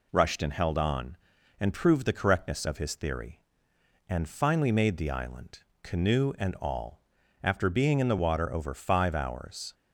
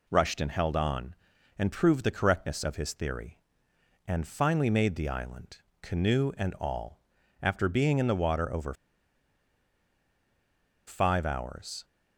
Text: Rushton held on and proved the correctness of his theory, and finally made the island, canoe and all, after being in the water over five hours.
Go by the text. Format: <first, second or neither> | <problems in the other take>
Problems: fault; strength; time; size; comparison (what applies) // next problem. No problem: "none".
first | pauses between "over" and "five"; strong; at 8.7 s; 2.1 s long